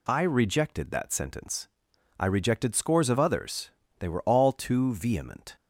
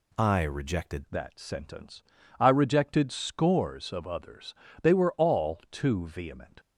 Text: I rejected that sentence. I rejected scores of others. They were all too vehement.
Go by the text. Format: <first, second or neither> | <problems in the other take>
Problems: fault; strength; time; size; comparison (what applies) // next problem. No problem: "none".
first | changes voice at "that"; from 1.0 s on; 5.5 s long